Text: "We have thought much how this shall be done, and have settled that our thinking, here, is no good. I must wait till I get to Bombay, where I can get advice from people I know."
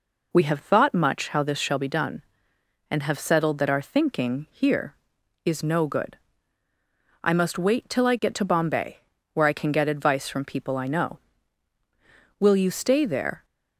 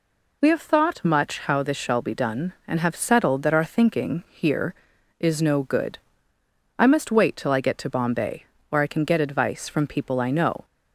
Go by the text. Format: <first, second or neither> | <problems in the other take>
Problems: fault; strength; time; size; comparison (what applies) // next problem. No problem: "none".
second | goes on to say "Will you stay there"; noticeable; from 12.4 s on; 1.0 s long